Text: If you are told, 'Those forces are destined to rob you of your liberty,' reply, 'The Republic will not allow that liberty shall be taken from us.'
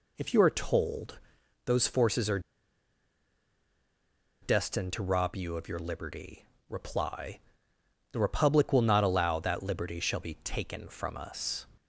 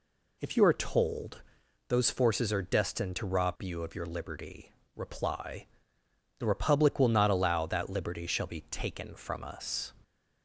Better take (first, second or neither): second